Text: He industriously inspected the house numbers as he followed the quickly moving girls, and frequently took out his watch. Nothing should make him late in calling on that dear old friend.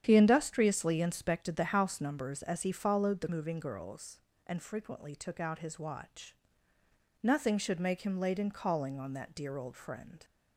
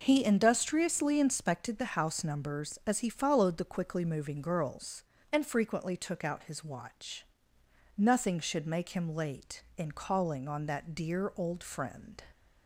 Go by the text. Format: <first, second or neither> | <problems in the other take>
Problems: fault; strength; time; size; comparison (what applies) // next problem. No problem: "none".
second | starts louder than the rest; strong; until 1.0 s; 9 dB // skips "quickly"; at 3.2 s